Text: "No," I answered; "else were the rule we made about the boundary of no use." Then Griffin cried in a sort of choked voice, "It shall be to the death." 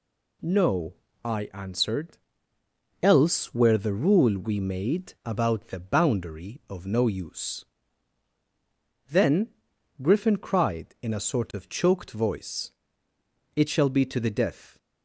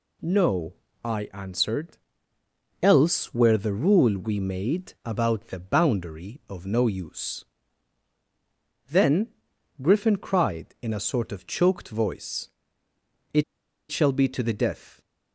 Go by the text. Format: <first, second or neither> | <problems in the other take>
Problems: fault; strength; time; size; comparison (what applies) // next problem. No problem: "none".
first | pauses between "Then" and "Griffin"; noticeable; at 9.3 s; 0.48 s long; noticeable in the first // pauses between "It" and "shall"; noticeable; at 13.4 s; 0.46 s long